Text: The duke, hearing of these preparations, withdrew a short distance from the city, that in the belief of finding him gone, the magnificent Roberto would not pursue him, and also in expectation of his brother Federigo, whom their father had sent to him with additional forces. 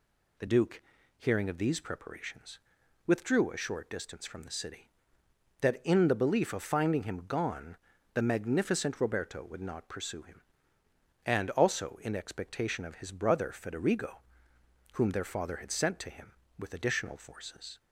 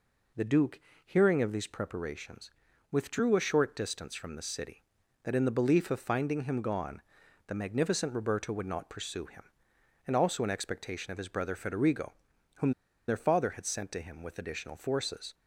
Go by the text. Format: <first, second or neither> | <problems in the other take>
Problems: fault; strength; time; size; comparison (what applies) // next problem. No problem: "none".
first | pauses between "whom" and "their"; at 12.7 s; 0.36 s long